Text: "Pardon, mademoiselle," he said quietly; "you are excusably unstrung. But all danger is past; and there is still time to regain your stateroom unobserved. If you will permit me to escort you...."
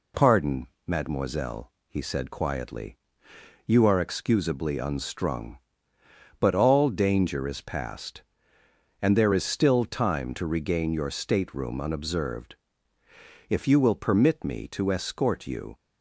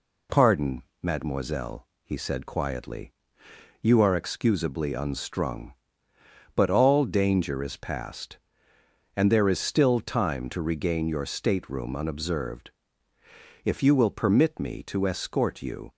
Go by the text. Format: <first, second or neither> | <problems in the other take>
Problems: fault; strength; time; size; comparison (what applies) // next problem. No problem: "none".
neither | none